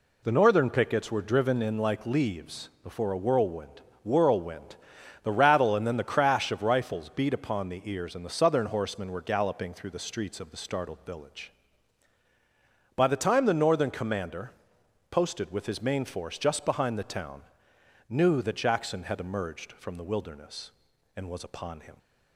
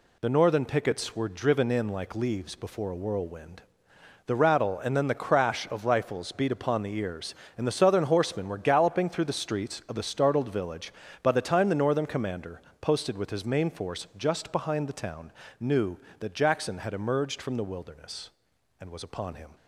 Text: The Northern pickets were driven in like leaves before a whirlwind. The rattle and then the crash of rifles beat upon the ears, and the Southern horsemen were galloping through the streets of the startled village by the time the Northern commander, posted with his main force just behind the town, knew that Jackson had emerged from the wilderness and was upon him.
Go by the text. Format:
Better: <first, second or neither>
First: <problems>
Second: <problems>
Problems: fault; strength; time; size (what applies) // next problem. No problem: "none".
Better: second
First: says "whirlwind" twice; at 4.0 s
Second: none